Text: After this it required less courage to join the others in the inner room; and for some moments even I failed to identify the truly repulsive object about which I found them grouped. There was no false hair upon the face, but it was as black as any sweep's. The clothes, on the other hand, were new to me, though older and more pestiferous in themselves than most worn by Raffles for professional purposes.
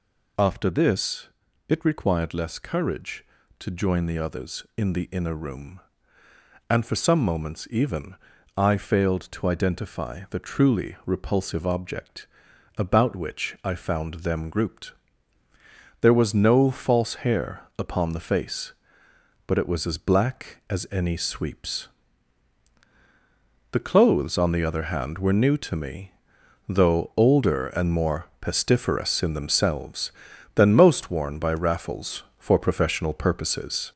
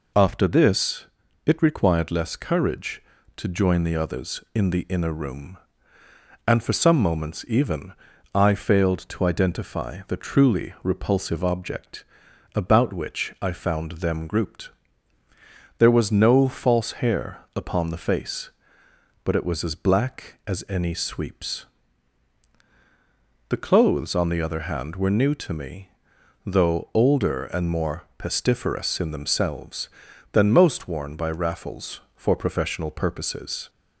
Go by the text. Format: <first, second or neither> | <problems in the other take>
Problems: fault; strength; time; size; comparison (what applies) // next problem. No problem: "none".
second | gets louder; noticeable; throughout; 4.5 dB // pauses between "this" and "it"; at 1.2 s; 0.40 s long; also in the second // pauses between "even" and "I"; at 8.1 s; 0.40 s long; also in the second // pauses between "object" and "about"; noticeable; at 12.2 s; 0.50 s long; noticeable in the second // pauses between "more" and "pestiferous"; slight; at 28.2 s; 0.16 s long; slight in the second